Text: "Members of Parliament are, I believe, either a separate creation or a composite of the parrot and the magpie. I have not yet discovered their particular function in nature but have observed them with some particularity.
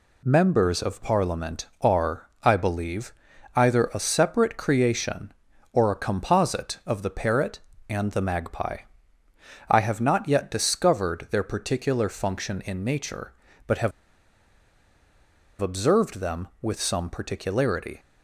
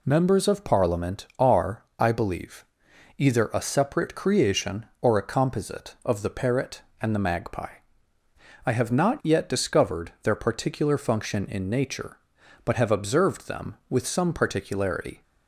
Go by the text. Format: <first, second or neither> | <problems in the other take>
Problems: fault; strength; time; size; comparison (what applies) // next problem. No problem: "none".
second | pauses between "have" and "observed"; strong; at 13.9 s; 1.7 s long